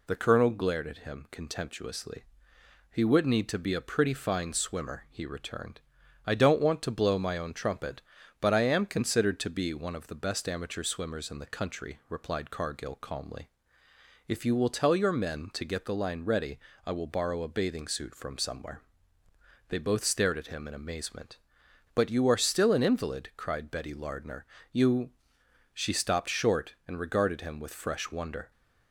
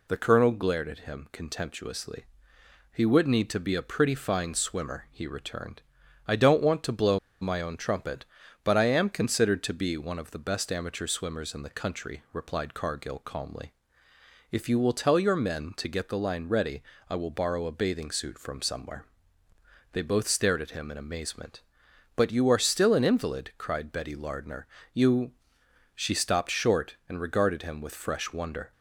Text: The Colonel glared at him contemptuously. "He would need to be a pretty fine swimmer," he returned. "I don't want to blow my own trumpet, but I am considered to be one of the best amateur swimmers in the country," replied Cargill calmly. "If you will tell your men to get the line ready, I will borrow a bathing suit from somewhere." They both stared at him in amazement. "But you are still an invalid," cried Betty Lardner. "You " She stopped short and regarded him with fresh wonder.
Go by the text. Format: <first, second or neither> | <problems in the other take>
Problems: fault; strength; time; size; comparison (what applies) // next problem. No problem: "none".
first | pauses between "blow" and "my"; slight; at 7.1 s; 0.22 s long